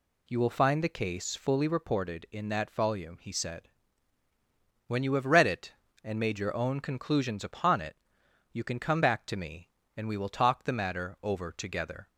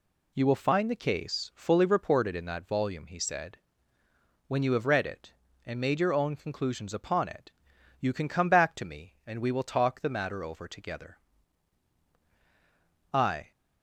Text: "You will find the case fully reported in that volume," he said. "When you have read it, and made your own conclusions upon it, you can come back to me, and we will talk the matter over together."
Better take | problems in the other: first | goes on to say "I"; slight; from 13.1 s on; 0.38 s long

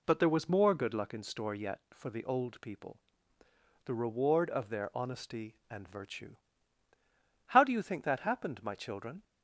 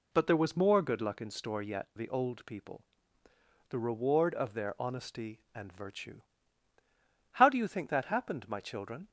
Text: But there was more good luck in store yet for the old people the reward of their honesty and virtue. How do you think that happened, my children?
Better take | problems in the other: first | skips "for"; at 1.9 s // pauses between "people" and "the"; noticeable; at 2.8 s; 0.88 s long; noticeable in the first

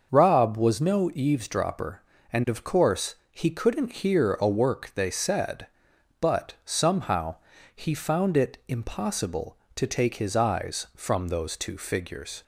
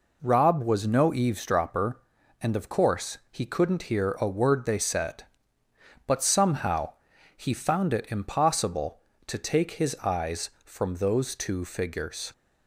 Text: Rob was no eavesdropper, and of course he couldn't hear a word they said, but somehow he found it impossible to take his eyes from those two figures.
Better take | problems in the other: second | starts louder than the rest; noticeable; until 1.1 s; 6 dB // pauses between "course" and "he"; slight; at 3.1 s; 0.16 s long // says "work" for "word"; at 4.4 s // pauses between "somehow" and "he"; at 7.3 s; 0.38 s long; also in the second

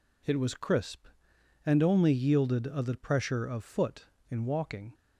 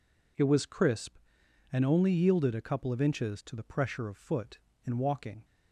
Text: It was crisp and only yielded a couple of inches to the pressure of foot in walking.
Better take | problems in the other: second | skips "couple of inches to"; at 2.8 s

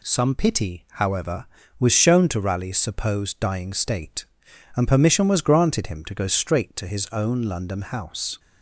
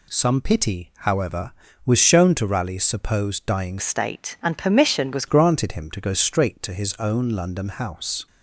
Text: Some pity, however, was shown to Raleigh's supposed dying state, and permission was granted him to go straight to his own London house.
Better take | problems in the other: first | changes voice from "state" to "was"; from 3.7 to 5.2 s; 1.5 s long

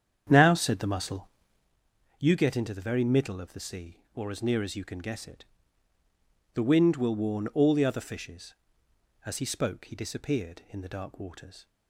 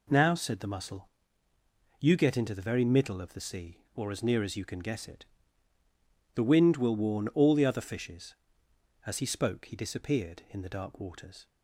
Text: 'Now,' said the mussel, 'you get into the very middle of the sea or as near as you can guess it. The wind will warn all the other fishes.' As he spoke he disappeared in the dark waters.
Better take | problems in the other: second | starts louder than the rest; strong; until 1.7 s; 8.5 dB

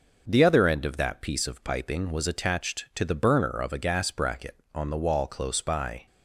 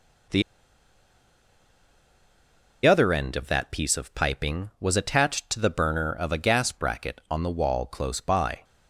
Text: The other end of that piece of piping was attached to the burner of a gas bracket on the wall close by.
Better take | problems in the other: first | pauses between "The" and "other"; strong; at 0.4 s; 2.4 s long

